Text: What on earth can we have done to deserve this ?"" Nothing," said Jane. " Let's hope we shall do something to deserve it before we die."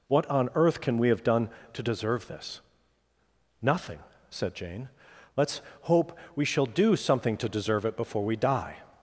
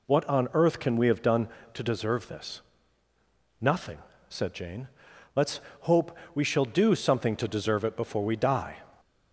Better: neither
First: pauses between "Let's" and "hope"; slight; at 5.6 s; 0.20 s long // pauses between "hope" and "we"; slight; at 6.1 s; 0.20 s long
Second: pauses between "Let's" and "hope"; slight; at 5.6 s; 0.20 s long // pauses between "hope" and "we"; slight; at 6.1 s; 0.20 s long

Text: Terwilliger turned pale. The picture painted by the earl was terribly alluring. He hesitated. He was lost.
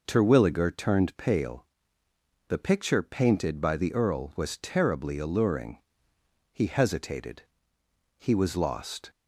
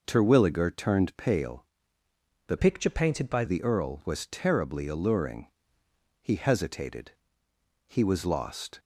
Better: first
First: none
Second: changes voice from "picture" to "by"; from 2.5 to 3.4 s; 0.9 s long

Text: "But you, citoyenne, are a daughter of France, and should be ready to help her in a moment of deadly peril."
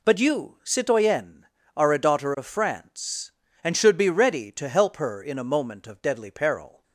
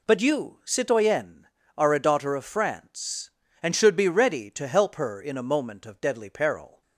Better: neither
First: none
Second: none

